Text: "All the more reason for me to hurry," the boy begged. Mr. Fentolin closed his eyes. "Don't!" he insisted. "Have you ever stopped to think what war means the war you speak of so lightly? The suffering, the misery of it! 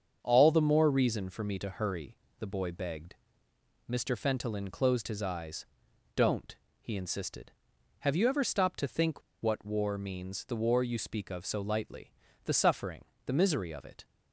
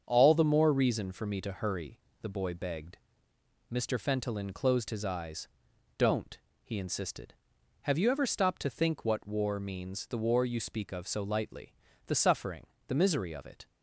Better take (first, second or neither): second